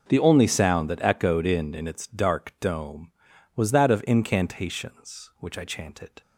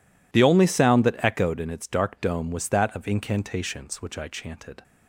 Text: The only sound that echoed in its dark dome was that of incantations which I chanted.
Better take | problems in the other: second | says "in" twice; at 1.7 s

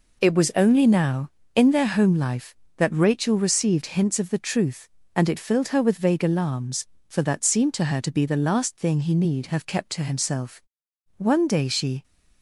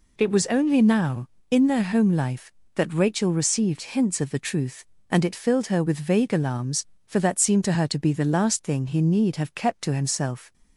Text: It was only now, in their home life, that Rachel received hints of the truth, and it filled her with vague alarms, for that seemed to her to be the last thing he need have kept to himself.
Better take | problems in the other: second | goes on to say "One day she"; noticeable; from 11.1 s on; 0.86 s long

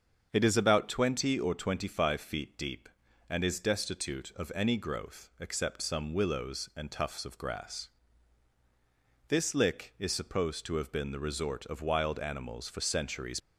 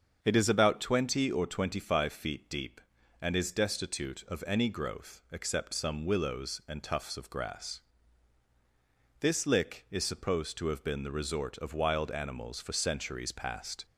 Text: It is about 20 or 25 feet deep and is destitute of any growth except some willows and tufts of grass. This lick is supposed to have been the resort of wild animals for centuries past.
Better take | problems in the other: second | starts louder than the rest; until 1.3 s; 7 dB; strong in the second // stops before "past"; at 13.3 s

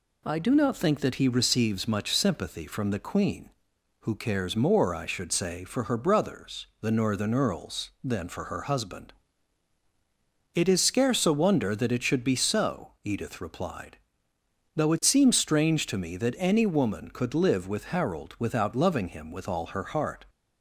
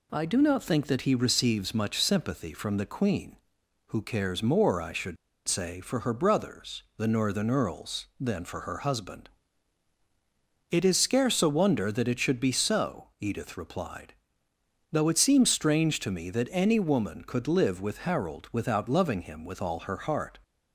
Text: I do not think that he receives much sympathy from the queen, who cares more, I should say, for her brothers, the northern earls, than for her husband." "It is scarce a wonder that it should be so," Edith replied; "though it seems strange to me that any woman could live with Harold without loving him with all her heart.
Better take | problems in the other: first | pauses between "should" and "say"; slight; at 5.1 s; 0.32 s long

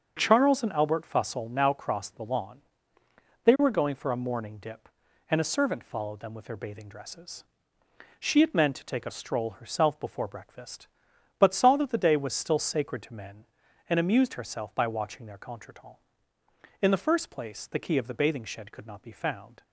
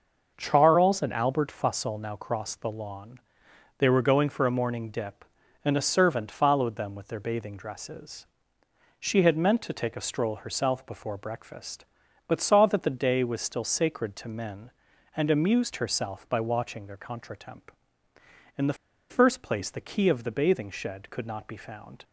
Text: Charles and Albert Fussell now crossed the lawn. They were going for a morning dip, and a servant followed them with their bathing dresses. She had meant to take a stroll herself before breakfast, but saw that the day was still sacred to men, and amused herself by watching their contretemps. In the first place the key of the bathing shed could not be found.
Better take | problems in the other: first | starts louder than the rest; noticeable; until 1.3 s; 6 dB; also in the first // pauses between "the" and "first"; slight; at 18.7 s; 0.35 s long

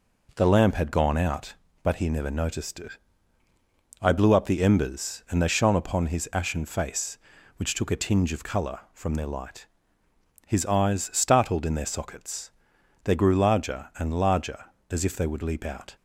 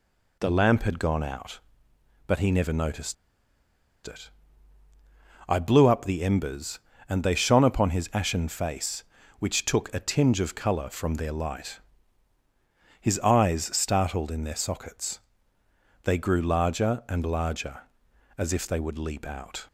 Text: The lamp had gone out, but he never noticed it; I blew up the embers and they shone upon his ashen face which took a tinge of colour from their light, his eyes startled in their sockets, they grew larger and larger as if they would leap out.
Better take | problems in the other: first | pauses between "noticed" and "it"; noticeable; at 3.1 s; 0.92 s long

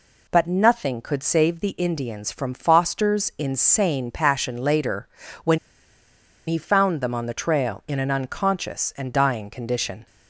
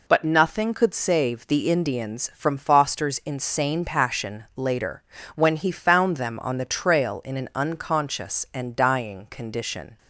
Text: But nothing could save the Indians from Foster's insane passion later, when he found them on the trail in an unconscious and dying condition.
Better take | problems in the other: second | pauses between "when" and "he"; noticeable; at 5.5 s; 0.89 s long

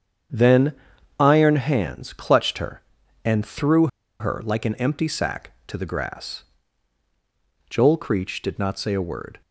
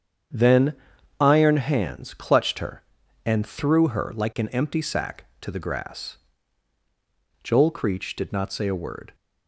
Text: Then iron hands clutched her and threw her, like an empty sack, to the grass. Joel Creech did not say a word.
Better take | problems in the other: second | starts louder than the rest; strong; until 1.7 s; 8 dB; strong in the second // pauses between "Then" and "iron"; noticeable; at 0.7 s; 0.46 s long; noticeable in the second // pauses between "threw" and "her"; slight; at 3.8 s; 0.33 s long

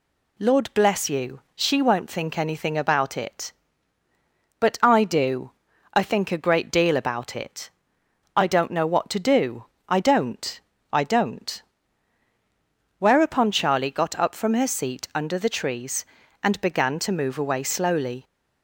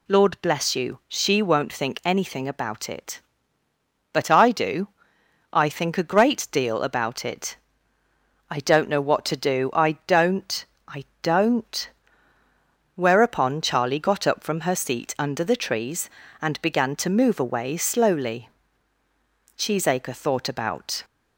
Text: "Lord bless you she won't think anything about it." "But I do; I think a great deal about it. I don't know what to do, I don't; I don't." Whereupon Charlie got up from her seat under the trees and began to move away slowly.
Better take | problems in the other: first | pauses between "I" and "don't"; slight; at 11.0 s; 0.16 s long // goes on to say "Cheesacre thought about"; from 19.5 s on; 1.4 s long

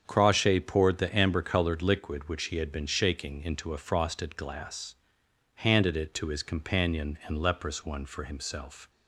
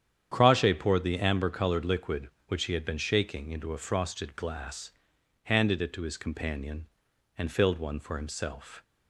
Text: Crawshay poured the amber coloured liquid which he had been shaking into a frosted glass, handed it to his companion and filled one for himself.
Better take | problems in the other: second | starts louder than the rest; strong; until 1.0 s; 8 dB; strong in the second // says "leprous" for "filled"; at 7.3 s

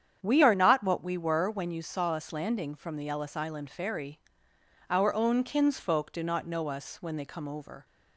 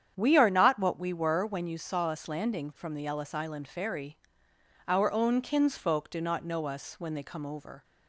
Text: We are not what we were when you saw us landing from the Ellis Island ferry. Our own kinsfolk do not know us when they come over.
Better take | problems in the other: neither | starts louder than the rest; strong; the same in both

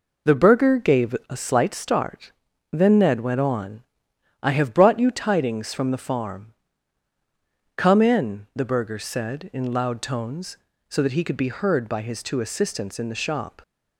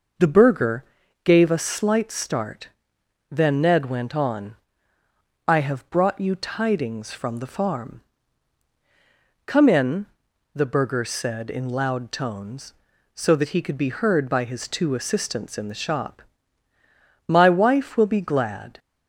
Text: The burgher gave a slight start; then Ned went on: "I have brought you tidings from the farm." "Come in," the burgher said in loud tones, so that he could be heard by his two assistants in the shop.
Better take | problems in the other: first | pauses between "burgher" and "gave"; at 0.8 s; 0.40 s long // goes on to say "My wife will be glad"; from 17.2 s on; 1.5 s long

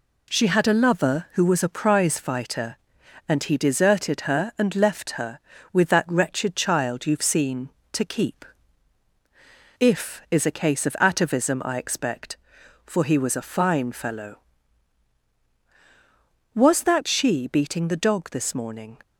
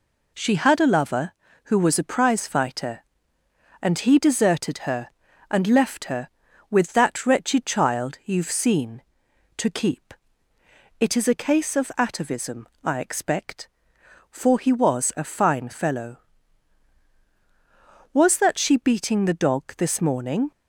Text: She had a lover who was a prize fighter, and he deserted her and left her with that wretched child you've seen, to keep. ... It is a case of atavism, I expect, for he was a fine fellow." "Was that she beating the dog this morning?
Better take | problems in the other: second | says "If" for "It"; at 9.7 s

